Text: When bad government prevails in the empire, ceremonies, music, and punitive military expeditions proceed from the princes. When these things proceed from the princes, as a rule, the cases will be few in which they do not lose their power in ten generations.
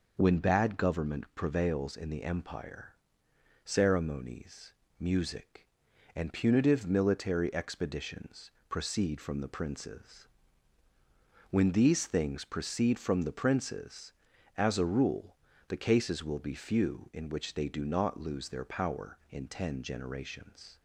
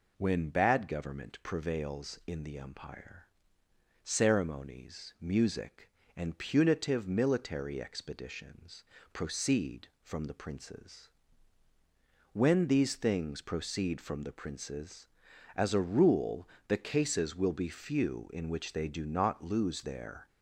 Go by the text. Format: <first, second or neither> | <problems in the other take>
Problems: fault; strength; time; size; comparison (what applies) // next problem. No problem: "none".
first | pauses between "expeditions" and "proceed"; slight; at 8.8 s; 0.28 s long; slight in the first // stops before "power in ten generations"; at 20.2 s